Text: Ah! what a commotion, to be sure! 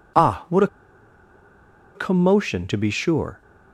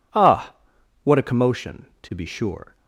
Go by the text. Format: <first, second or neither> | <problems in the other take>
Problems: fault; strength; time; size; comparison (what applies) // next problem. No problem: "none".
second | pauses between "a" and "commotion"; strong; at 0.6 s; 1.2 s long